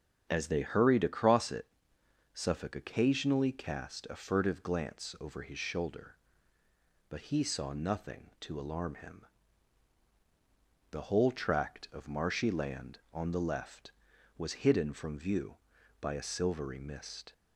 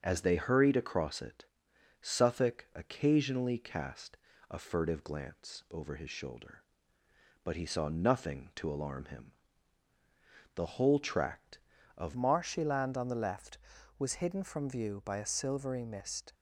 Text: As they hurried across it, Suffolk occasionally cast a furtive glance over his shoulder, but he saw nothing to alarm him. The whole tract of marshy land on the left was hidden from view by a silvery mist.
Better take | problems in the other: first | starts louder than the rest; until 1.0 s; 6.5 dB; also in the first // pauses between "cast" and "a"; slight; at 4.1 s; 0.32 s long // changes voice at "marshy"; from 12.1 s on; 4.2 s long

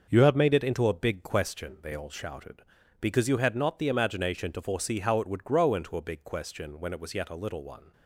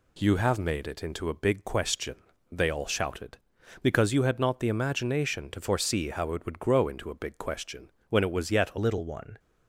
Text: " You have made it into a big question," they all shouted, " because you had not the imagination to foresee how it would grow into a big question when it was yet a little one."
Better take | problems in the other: first | pauses between "question" and "when"; slight; at 7.9 s; 0.18 s long // changes voice at "little"; from 8.7 s on; 0.6 s long

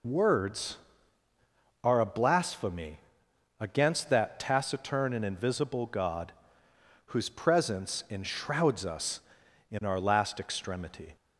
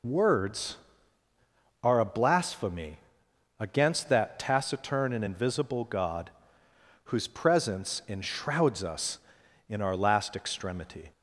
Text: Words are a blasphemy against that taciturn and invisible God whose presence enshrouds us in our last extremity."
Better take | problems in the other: neither | pauses between "blasphemy" and "against"; noticeable; the same in both // pauses between "God" and "whose"; noticeable; the same in both

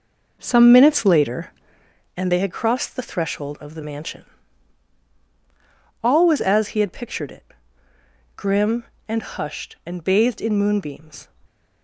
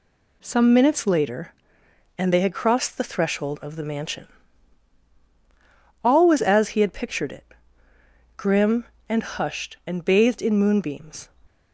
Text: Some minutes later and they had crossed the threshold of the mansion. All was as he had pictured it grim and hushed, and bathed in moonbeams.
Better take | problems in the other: second | starts louder than the rest; noticeable; until 2.0 s; 5 dB // pauses between "it" and "grim"; noticeable; at 7.4 s; 0.90 s long; noticeable in the second

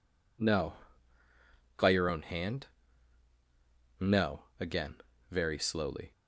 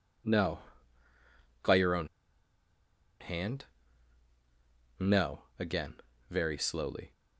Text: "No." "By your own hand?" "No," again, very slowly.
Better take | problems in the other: first | pauses between "own" and "hand"; at 2.0 s; 1.1 s long

